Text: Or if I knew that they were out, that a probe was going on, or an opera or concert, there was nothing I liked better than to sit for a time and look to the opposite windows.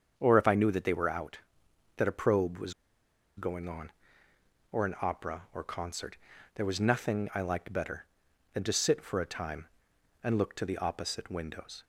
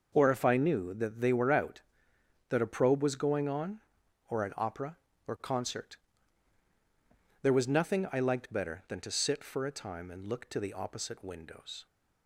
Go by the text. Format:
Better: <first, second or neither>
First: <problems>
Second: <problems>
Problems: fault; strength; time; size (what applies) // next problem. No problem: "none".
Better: second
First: starts louder than the rest; strong; until 1.1 s; 7.5 dB // pauses between "was" and "going"; noticeable; at 2.7 s; 0.64 s long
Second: none